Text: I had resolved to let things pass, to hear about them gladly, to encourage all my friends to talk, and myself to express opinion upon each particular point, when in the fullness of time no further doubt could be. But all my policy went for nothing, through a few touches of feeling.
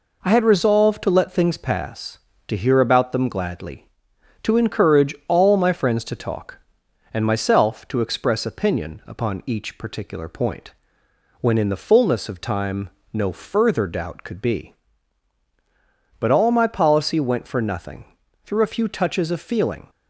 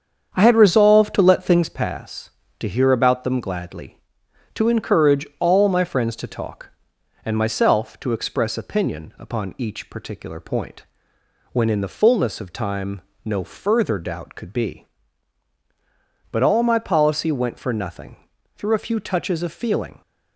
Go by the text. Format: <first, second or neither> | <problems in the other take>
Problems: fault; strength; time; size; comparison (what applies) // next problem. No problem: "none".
first | starts louder than the rest; strong; until 1.7 s; 7.5 dB // pauses between "time" and "no"; slight; at 13.0 s; 0.24 s long; slight in the first